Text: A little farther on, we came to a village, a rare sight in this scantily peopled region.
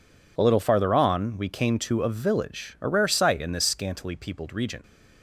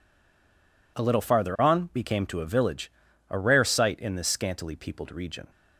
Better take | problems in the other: first | stays silent before the first word; slight; until 0.9 s; 0.9 s long

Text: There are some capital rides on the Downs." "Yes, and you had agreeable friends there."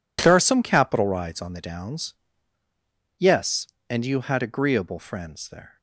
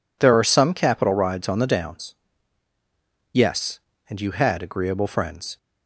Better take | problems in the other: first | stops before "there"; at 5.5 s

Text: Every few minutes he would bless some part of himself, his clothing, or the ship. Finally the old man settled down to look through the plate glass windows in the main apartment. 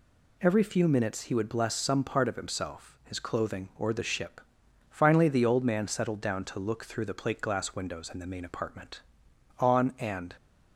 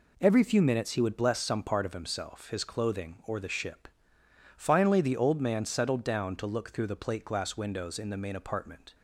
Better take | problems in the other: second | goes on to say "On and"; noticeable; from 9.5 s on; 0.78 s long

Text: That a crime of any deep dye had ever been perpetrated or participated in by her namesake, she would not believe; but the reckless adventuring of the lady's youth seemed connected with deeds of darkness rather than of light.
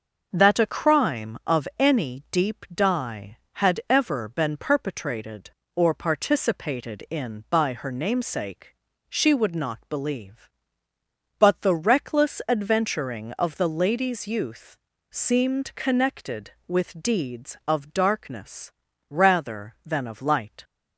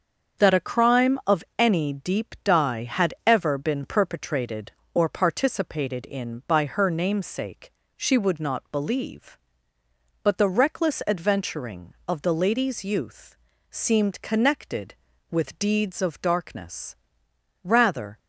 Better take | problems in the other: first | starts louder than the rest; until 1.6 s; 6.5 dB; also in the first // pauses between "youth" and "seemed"; slight; at 13.3 s; 0.34 s long; slight in the first // pauses between "darkness" and "rather"; noticeable; at 16.9 s; 0.66 s long; also in the first // stops before "than of light"; at 18.1 s

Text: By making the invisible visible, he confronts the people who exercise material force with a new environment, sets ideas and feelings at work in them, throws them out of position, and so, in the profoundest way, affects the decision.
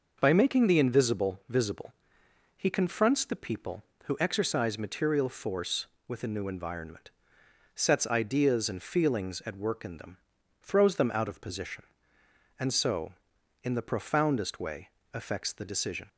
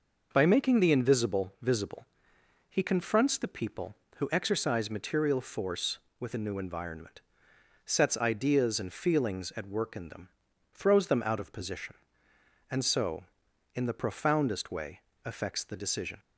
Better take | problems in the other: neither | none

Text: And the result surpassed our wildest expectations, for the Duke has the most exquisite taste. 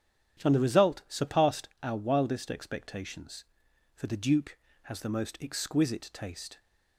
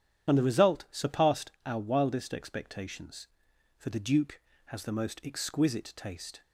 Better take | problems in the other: first | loses the start of "And"; at 0.2 s; 55 ms // starts louder than the rest; strong; until 1.3 s; 9.5 dB; strong in the first

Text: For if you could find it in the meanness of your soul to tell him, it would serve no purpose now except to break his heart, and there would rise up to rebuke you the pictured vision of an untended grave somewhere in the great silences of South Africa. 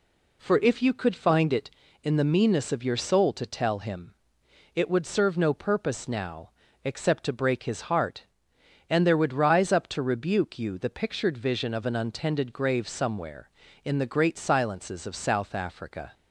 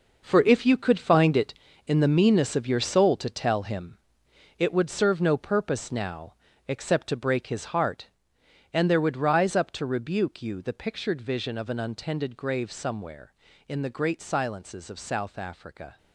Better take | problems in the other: first | gets quieter; strong; throughout; 11 dB // pauses between "now" and "except"; slight; at 6.3 s; 0.34 s long; slight in the first

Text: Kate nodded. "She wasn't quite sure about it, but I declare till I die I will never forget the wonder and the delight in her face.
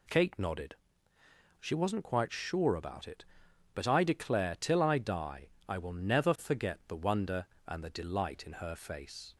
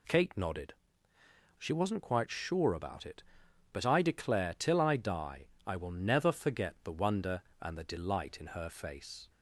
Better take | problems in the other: neither | pauses between "die" and "I"; slight; the same in both

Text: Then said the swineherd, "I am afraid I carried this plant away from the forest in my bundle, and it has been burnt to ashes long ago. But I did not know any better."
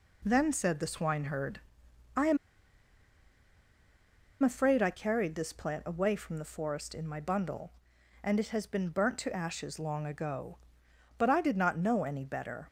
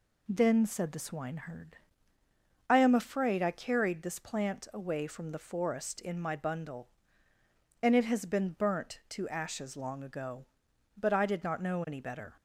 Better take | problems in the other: second | pauses between "am" and "afraid"; strong; at 2.3 s; 2.0 s long

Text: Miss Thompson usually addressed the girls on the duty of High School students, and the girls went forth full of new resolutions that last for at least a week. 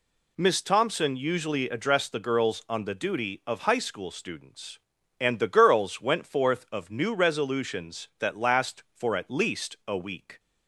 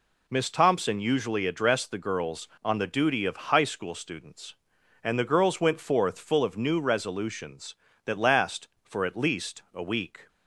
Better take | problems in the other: second | skips "full"; at 6.6 s

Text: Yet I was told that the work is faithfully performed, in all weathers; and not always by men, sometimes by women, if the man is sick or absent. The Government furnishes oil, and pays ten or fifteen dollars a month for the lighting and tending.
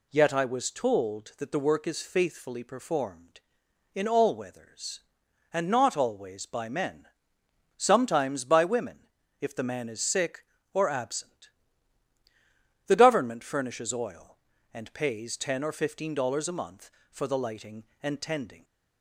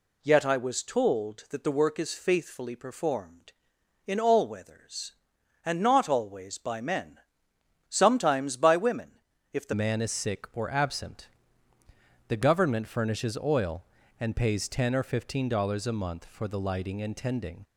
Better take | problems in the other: first | changes voice at "man"; from 9.7 s on; 7.9 s long

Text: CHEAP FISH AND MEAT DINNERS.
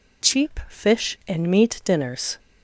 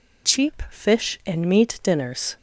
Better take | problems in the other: neither | none

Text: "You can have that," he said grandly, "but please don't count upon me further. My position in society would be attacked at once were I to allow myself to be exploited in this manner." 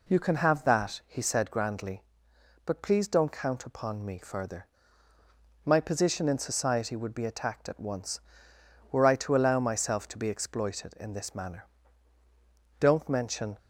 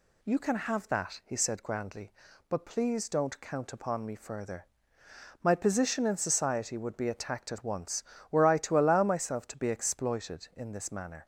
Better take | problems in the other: second | goes on to say "Don't mention"; noticeable; from 12.7 s on; 0.78 s long

